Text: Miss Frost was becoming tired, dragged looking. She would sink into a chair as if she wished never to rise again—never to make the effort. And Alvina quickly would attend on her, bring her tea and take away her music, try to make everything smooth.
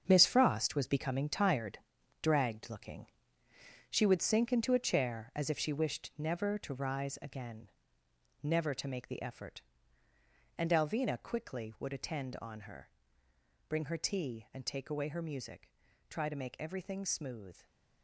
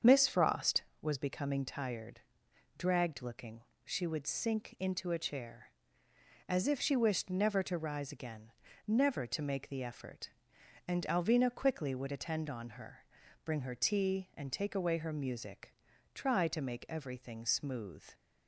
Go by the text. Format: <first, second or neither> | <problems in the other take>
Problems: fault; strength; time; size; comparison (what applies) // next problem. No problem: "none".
second | gets quieter; strong; throughout; 9.5 dB // starts louder than the rest; strong; until 1.0 s; 7 dB; strong in the second